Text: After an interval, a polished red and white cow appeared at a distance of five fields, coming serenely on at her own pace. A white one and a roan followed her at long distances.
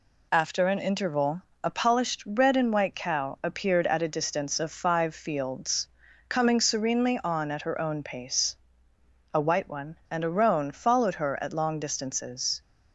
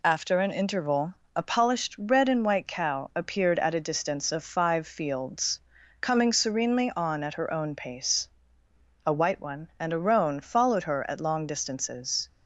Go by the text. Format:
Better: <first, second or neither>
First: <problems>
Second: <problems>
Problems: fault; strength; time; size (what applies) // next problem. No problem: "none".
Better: neither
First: none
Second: none